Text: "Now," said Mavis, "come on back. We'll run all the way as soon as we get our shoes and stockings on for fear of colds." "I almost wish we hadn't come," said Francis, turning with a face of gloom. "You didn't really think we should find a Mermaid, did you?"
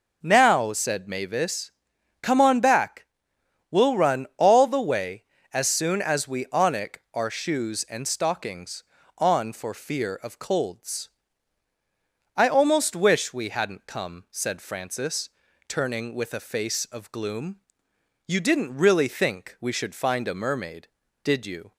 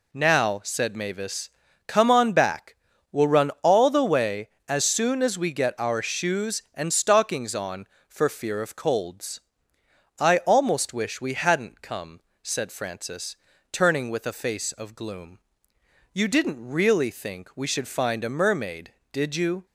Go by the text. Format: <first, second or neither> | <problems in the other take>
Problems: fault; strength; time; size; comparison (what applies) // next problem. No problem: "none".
second | says "onic" for "get"; at 6.4 s